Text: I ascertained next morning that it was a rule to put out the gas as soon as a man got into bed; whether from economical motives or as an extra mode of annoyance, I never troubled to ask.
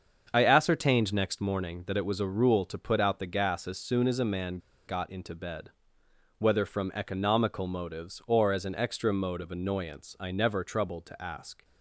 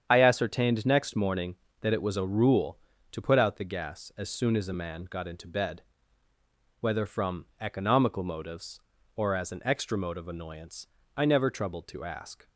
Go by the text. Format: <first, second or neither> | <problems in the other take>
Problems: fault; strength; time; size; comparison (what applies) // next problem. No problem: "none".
second | starts louder than the rest; until 1.3 s; 7 dB; strong in the second // pauses between "man" and "got"; slight; at 4.5 s; 0.29 s long